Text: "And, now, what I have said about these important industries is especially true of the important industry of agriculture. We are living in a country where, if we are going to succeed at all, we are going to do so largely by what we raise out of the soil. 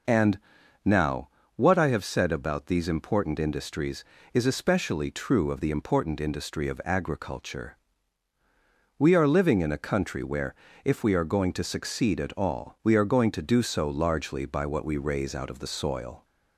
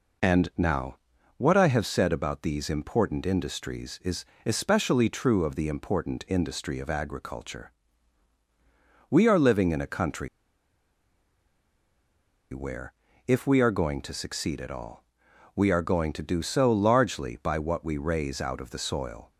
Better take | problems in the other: first | pauses between "is" and "especially"; slight; at 4.2 s; 0.20 s long // pauses between "country" and "where"; strong; at 10.2 s; 2.2 s long

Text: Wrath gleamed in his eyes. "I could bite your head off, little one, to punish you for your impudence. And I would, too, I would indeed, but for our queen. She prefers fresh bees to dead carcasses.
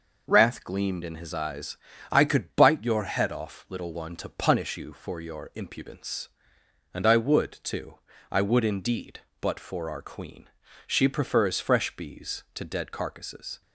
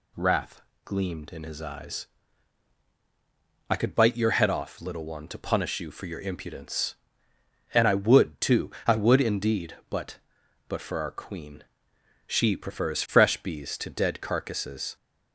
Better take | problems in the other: first | pauses between "Wrath" and "gleamed"; slight; at 0.6 s; 0.24 s long // says "but" twice; at 10.6 s

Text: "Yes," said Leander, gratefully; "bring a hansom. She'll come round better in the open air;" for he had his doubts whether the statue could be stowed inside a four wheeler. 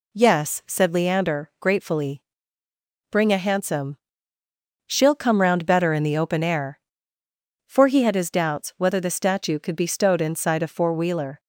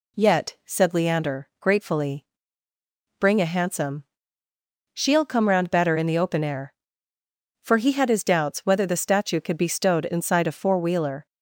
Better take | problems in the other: first | says "Yet" for "Yes"; at 0.1 s

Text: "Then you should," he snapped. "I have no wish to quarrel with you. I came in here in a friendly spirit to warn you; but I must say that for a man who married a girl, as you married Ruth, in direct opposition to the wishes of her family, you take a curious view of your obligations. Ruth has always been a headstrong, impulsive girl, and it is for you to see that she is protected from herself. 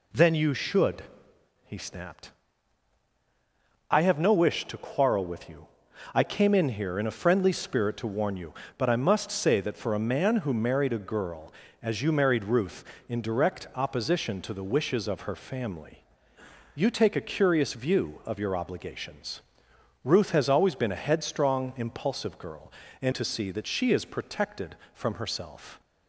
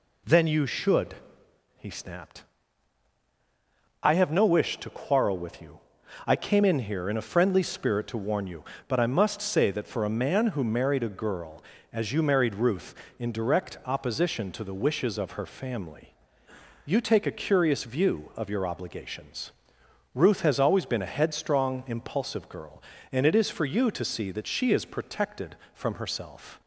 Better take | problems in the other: second | skips "it is for you"; at 23.1 s

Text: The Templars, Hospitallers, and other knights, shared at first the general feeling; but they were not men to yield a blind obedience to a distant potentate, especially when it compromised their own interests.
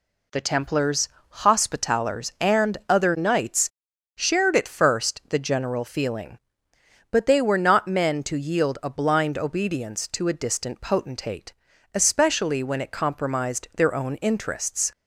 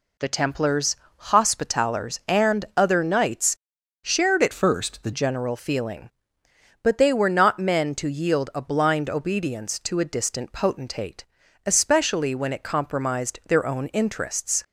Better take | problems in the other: first | changes voice from "first" to "the"; from 4.5 to 5.1 s; 0.6 s long

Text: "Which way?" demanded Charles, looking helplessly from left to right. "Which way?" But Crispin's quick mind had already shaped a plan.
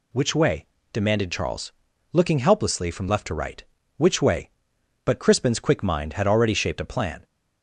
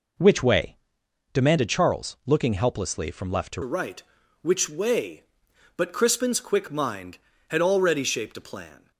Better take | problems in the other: first | changes voice at "right"; from 3.6 s on; 5.3 s long

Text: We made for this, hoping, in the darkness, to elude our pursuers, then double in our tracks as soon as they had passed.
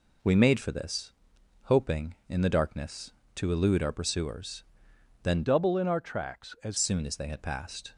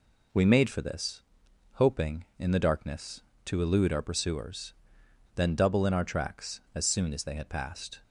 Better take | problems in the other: second | changes voice from "double" to "as"; from 5.4 to 6.7 s; 1.3 s long

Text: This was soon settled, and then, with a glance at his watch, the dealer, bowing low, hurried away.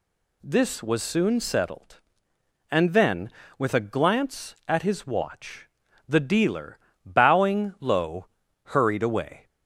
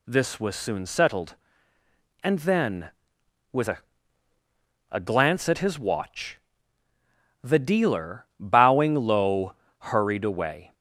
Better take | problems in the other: first | says "a" twice; at 4.9 s

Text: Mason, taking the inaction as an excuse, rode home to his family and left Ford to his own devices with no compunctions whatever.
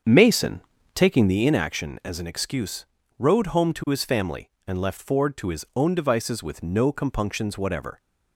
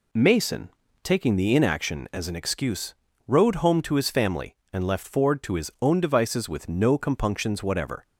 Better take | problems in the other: second | starts louder than the rest; strong; until 1.4 s; 7 dB

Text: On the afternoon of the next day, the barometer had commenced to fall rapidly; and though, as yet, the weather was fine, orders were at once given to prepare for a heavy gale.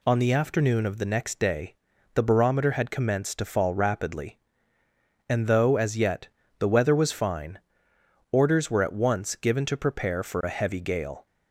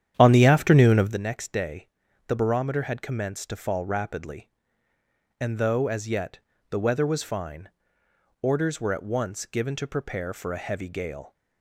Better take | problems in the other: first | starts louder than the rest; strong; until 1.2 s; 10 dB

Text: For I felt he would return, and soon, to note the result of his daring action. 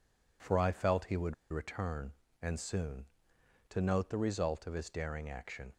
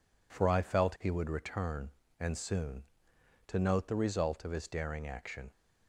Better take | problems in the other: second | pauses between "would" and "return"; slight; at 1.3 s; 0.16 s long

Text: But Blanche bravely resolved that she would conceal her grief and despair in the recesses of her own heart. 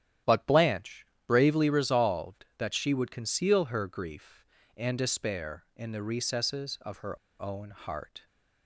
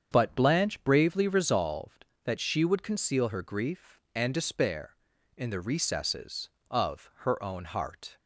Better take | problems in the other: second | starts louder than the rest; strong; until 1.4 s; 11 dB; strong in the second // pauses between "Blanche" and "bravely"; slight; at 1.0 s; 0.22 s long // pauses between "her" and "own"; slight; at 7.1 s; 0.23 s long

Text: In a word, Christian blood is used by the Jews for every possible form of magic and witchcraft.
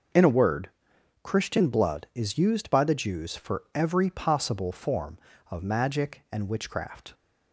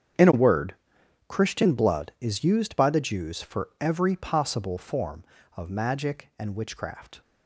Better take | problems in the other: first | gets quieter; strong; throughout; 16.5 dB

